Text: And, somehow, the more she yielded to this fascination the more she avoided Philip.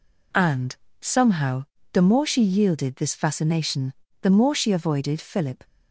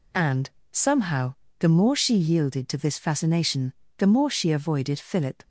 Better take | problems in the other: second | skips "to"; at 2.9 s // pauses between "fascination" and "the"; slight; at 3.9 s; 0.30 s long; slight in the second

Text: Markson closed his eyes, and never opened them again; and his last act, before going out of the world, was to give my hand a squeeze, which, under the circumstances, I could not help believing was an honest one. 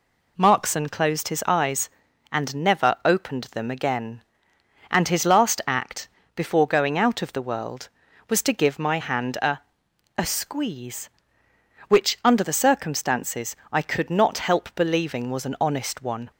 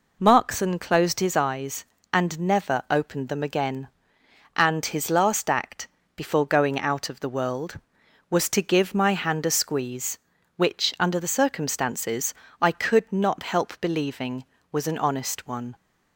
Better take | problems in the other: second | says "a" twice; at 10.1 s

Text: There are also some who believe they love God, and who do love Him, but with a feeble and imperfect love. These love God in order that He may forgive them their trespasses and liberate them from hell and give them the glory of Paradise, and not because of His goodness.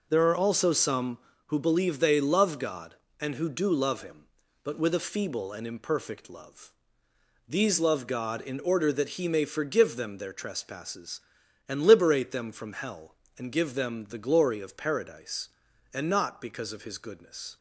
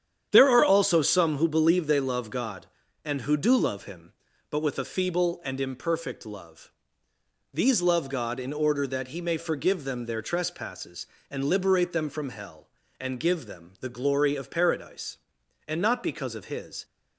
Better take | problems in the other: first | starts louder than the rest; strong; until 1.3 s; 9 dB // stops before "goodness"; at 16.8 s

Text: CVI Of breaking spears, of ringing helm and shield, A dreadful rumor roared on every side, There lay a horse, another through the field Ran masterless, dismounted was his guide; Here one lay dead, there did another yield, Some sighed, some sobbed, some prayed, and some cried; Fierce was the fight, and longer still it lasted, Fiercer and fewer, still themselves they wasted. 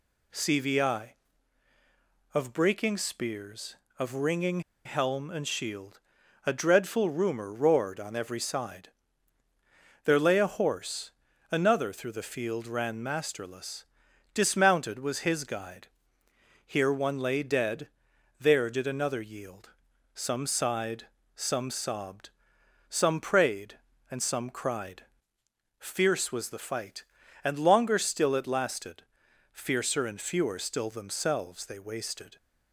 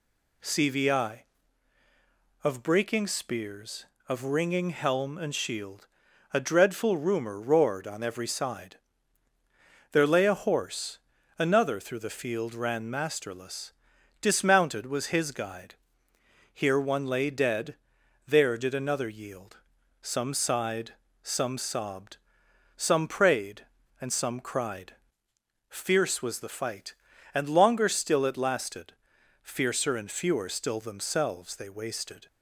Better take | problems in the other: second | pauses between "ringing" and "helm"; slight; at 4.6 s; 0.25 s long

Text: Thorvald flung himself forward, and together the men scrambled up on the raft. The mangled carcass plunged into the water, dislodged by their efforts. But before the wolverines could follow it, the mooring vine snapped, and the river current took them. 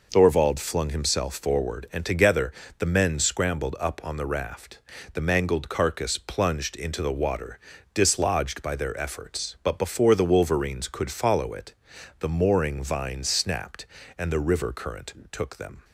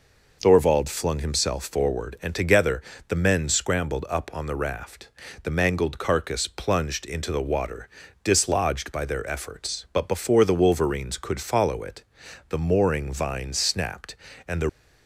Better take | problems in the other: first | pauses between "together" and "the"; slight; at 2.8 s; 0.28 s long; slight in the first // stops before "river current took them"; at 14.6 s

